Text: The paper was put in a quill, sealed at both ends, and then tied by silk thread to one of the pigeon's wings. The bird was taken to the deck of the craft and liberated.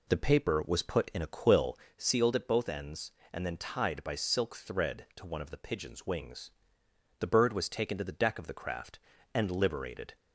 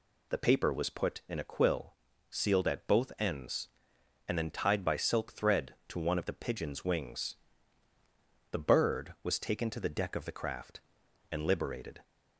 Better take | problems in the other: second | starts louder than the rest; slight; until 2.0 s; 3 dB

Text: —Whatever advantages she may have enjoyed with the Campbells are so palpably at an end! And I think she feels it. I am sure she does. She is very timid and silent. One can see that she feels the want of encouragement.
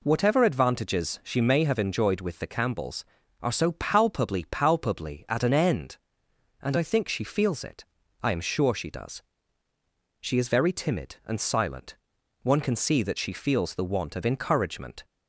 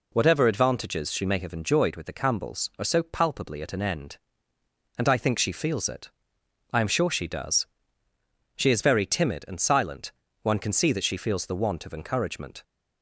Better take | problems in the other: second | says "palpably" twice; at 4.5 s

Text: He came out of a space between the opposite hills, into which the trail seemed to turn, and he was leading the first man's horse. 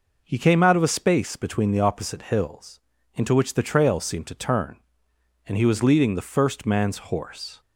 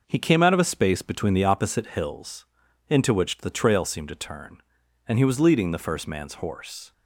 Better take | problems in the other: neither | none

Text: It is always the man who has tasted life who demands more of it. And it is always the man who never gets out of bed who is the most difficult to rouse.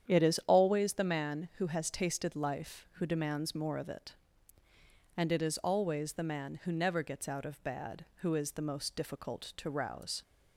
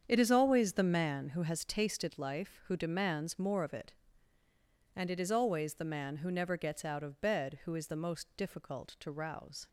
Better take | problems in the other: second | starts louder than the rest; strong; until 1.1 s; 9 dB; strong in the second // says "bad" for "bed"; at 7.6 s

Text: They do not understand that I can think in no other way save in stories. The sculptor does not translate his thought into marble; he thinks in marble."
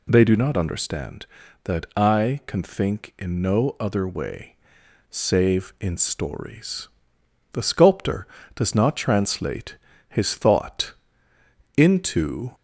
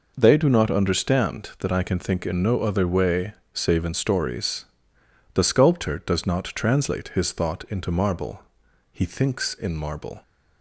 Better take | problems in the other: second | pauses between "way" and "save"; noticeable; at 4.5 s; 0.56 s long; slight in the second // pauses between "translate" and "his"; slight; at 9.7 s; 0.32 s long // pauses between "thought" and "into"; noticeable; at 10.9 s; 0.84 s long // stops before "marble he thinks in marble"; at 12.5 s

